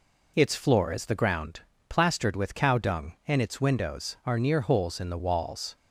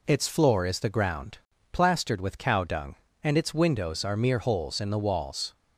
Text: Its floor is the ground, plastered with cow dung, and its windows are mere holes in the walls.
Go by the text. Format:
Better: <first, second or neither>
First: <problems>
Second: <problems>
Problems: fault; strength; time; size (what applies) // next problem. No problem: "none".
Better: second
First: says "near" for "mere"; at 4.3 s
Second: none